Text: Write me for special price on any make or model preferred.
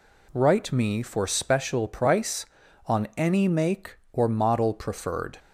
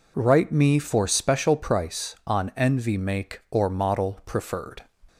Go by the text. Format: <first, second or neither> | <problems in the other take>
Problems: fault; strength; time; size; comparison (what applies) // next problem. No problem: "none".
first | says "envy" for "any"; at 2.5 s